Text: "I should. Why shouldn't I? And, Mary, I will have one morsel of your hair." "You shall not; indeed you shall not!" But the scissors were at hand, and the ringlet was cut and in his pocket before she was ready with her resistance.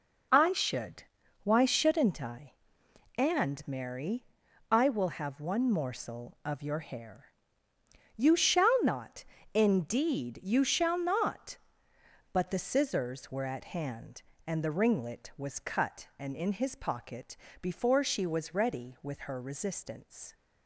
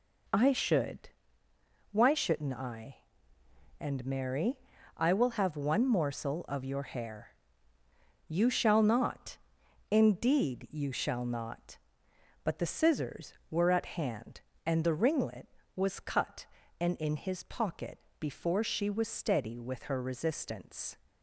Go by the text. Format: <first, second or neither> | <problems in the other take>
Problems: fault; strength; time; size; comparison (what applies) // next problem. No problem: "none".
first | pauses between "pocket" and "before"; slight; at 17.9 s; 0.20 s long; slight in the first // says "steady" for "ready"; at 19.0 s